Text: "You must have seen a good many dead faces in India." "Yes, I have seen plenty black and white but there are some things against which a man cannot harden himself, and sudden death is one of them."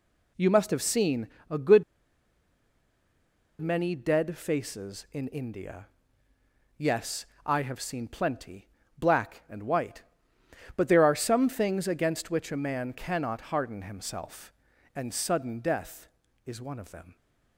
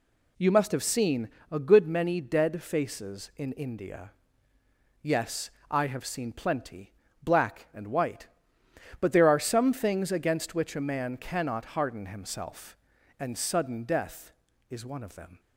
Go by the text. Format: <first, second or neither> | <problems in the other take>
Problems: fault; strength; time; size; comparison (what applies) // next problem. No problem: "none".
second | pauses between "seen" and "a"; slight; at 1.2 s; 0.20 s long; slight in the second // pauses between "good" and "many"; strong; at 1.8 s; 1.7 s long // pauses between "plenty" and "black"; slight; at 8.6 s; 0.30 s long; slight in the second